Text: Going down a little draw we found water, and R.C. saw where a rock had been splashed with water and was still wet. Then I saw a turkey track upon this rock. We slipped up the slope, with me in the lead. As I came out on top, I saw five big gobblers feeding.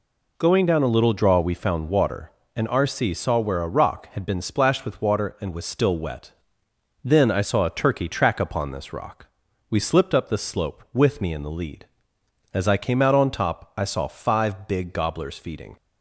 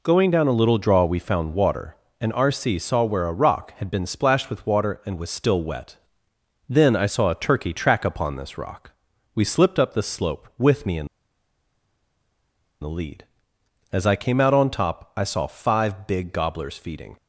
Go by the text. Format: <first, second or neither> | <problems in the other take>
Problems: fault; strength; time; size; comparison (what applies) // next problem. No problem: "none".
first | pauses between "in" and "the"; strong; at 11.0 s; 1.7 s long